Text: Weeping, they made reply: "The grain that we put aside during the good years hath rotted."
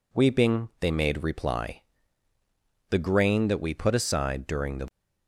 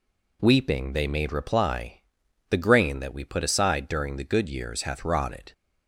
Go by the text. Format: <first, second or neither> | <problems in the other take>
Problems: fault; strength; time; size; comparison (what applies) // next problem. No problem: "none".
second | stops before "good years hath rotted"; at 4.8 s